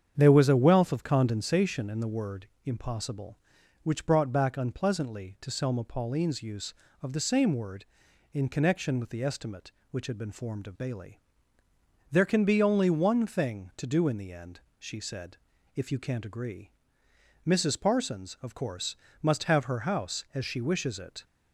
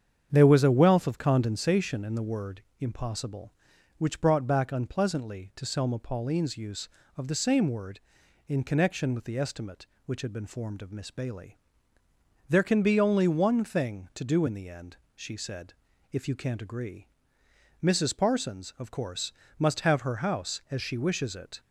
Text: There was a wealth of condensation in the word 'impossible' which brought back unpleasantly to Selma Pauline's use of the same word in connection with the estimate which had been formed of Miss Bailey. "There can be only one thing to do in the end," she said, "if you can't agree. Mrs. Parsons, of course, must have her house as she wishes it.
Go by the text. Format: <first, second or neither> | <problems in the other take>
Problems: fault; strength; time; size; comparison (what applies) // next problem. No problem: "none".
second | starts louder than the rest; strong; until 1.1 s; 8 dB; strong in the second // pauses between "word" and "impossible"; slight; at 2.4 s; 0.18 s long; slight in the second // skips "Miss"; at 10.7 s